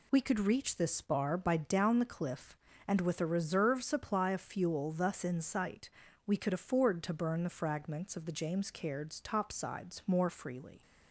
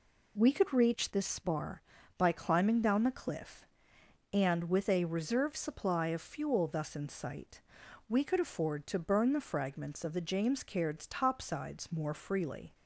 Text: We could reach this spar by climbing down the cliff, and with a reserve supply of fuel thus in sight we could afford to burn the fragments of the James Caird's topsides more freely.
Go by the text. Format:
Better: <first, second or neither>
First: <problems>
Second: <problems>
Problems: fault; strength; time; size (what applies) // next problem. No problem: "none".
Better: second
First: skips "climbing"; at 1.5 s // pauses between "sight" and "we"; slight; at 5.9 s; 0.34 s long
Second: pauses between "sight" and "we"; at 7.6 s; 0.44 s long